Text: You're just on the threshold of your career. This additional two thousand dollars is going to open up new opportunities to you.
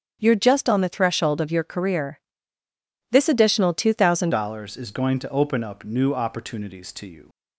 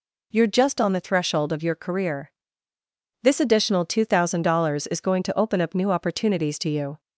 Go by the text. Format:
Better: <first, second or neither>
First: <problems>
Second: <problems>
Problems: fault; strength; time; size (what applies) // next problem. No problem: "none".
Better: second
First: starts louder than the rest; strong; until 1.2 s; 8 dB // changes voice at "dollars"; from 4.3 s on; 2.9 s long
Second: none